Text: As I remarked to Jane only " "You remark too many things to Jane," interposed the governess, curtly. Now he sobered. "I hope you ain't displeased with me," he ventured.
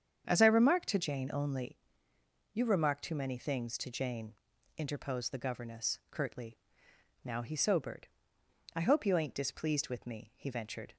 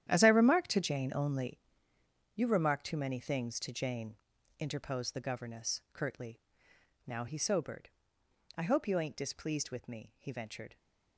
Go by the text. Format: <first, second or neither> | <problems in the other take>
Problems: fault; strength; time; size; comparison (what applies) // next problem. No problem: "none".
first | gets quieter; strong; throughout; 8 dB // starts louder than the rest; strong; until 1.1 s; 10.5 dB; strong in the first